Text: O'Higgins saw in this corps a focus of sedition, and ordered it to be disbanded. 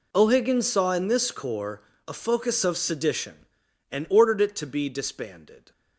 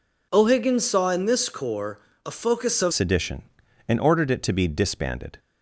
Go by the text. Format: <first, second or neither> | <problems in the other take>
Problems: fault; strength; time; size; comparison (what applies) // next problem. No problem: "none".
first | pauses between "corps" and "a"; slight; at 1.9 s; 0.28 s long; slight in the first // changes voice at "sedition"; from 2.9 s on; 2.4 s long